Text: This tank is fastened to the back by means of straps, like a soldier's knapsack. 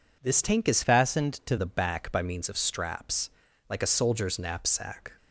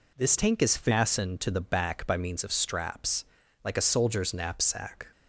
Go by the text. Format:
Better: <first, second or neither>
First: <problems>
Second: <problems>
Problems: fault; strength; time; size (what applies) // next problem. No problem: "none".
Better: second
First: changes voice from "fastened" to "to"; from 0.8 to 1.5 s; 0.7 s long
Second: none